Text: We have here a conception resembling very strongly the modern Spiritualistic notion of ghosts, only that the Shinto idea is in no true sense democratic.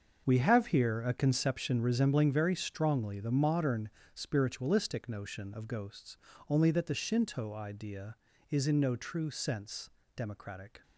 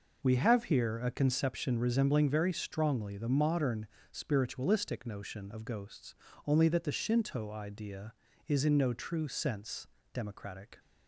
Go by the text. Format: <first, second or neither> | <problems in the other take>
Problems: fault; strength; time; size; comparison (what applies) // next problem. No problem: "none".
second | gets quieter; strong; throughout; 11.5 dB // pauses between "modern" and "Spiritualistic"; slight; at 3.8 s; 0.22 s long; slight in the second // pauses between "sense" and "democratic"; slight; at 9.8 s; 0.26 s long; slight in the second